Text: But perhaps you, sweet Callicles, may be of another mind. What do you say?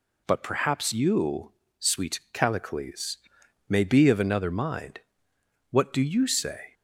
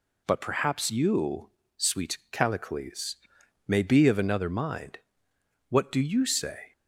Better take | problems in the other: neither | none

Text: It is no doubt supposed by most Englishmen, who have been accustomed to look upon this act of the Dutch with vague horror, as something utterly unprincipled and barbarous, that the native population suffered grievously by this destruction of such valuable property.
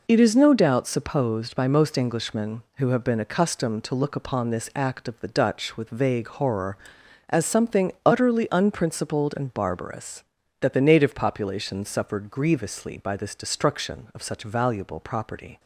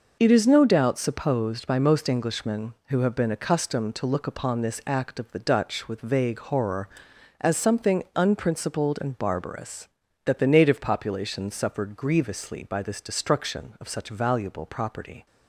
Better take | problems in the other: first | skips "utterly"; at 8.0 s

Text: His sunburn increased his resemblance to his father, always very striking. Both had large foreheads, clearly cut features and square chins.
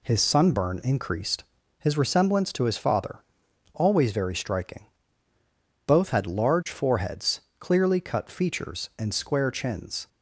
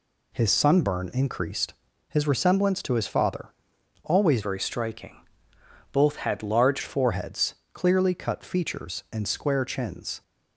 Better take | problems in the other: first | pauses between "increased" and "his"; slight; at 1.7 s; 0.36 s long; slight in the first // changes voice from "very" to "large"; from 4.4 to 6.8 s; 2.4 s long

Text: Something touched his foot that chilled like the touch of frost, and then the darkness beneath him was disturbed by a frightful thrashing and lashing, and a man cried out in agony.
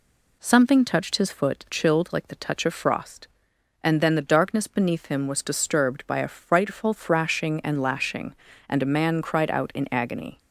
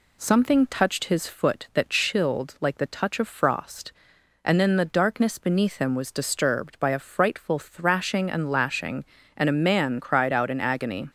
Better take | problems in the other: second | skips "that"; at 1.6 s

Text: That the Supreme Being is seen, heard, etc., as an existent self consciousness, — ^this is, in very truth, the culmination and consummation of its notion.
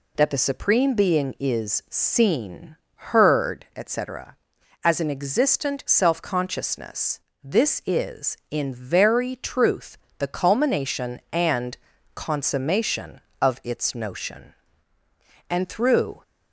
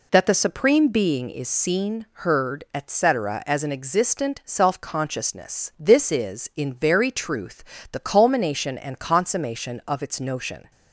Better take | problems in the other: second | pauses between "and" and "consummation"; at 11.7 s; 0.38 s long // goes on to say "And through"; noticeable; from 15.5 s on; 0.72 s long

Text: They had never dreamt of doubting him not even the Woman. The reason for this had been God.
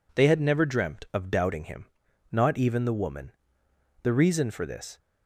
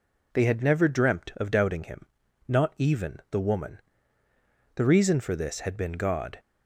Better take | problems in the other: second | pauses between "him" and "not"; noticeable; at 1.8 s; 0.46 s long; also in the second // stops before "had been God"; at 4.9 s

